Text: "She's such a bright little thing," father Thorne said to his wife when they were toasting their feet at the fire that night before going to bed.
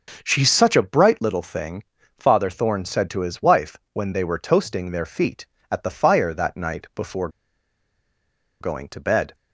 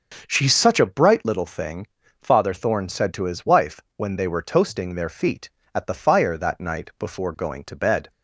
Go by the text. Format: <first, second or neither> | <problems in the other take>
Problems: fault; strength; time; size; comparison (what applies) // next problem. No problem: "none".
second | starts louder than the rest; until 1.2 s; 6.5 dB; also in the second // pauses between "wife" and "when"; slight; at 3.7 s; 0.16 s long; slight in the second // pauses between "before" and "going"; strong; at 7.2 s; 1.3 s long